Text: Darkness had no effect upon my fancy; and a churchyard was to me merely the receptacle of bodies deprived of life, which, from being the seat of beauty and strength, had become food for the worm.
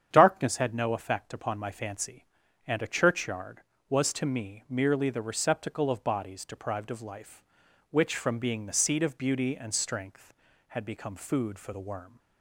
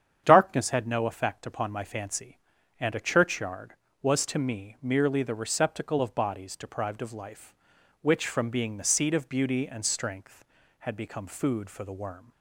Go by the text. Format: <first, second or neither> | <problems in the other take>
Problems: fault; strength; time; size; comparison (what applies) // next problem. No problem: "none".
neither | starts louder than the rest; strong; the same in both